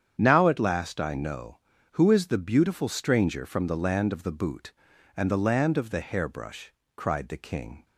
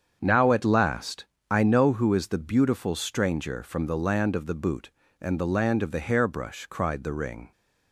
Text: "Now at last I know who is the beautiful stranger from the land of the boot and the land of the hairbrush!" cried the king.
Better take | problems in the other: first | starts louder than the rest; strong; until 1.2 s; 7.5 dB; strong in the first // pauses between "last" and "I"; slight; at 1.2 s; 0.24 s long // says "ring" for "king"; at 7.1 s

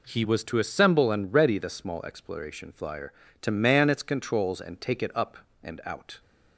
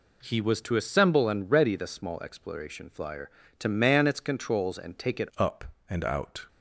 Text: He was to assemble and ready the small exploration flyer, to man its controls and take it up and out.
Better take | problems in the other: first | changes voice at "up"; from 5.3 s on; 1.1 s long

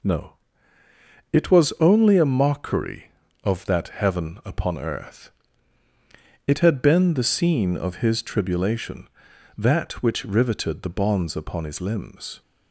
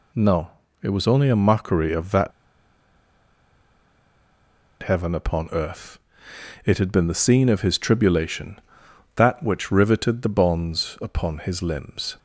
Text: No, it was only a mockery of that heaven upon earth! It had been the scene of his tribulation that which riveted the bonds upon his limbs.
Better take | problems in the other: first | pauses between "that" and "heaven"; strong; at 2.3 s; 2.5 s long

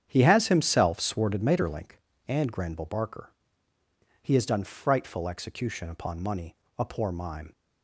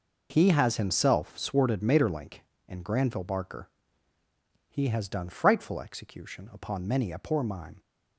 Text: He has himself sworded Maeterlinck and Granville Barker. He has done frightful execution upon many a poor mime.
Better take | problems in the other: second | starts louder than the rest; strong; until 1.1 s; 8.5 dB // says "money" for "many"; at 6.2 s

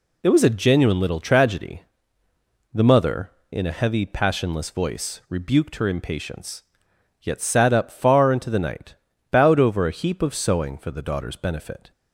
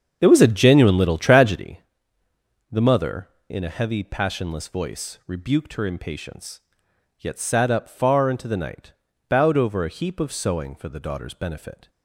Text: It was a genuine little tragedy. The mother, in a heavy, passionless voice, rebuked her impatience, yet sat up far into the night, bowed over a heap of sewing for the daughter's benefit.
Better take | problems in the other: first | starts louder than the rest; strong; until 1.7 s; 7.5 dB

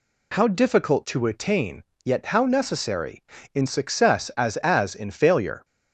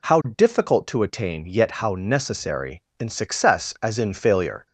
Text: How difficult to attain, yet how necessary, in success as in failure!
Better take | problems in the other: second | says "as" twice; at 4.5 s

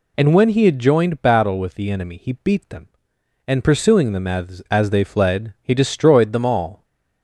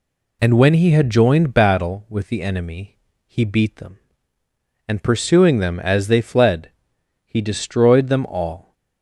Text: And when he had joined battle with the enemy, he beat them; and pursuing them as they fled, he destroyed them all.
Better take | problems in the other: second | says "as" twice; at 4.7 s

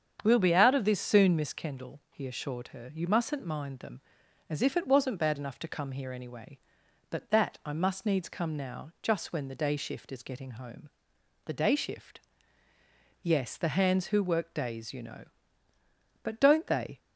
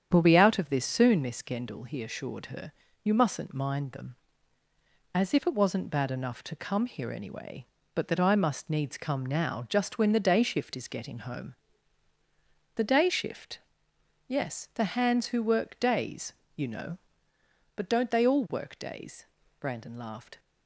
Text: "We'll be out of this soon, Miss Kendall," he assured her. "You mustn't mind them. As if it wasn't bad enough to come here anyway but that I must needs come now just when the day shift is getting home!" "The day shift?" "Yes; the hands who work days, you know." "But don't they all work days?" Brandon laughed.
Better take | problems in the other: second | starts louder than the rest; strong; until 1.2 s; 8 dB; strong in the second // stops before "all work days Brandon laughed"; at 16.9 s

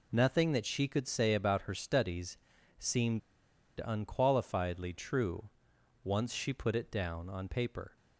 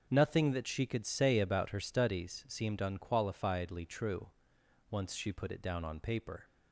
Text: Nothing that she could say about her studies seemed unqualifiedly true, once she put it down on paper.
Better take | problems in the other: second | pauses between "studies" and "seemed"; at 2.3 s; 0.40 s long // pauses between "seemed" and "unqualifiedly"; noticeable; at 3.2 s; 0.65 s long

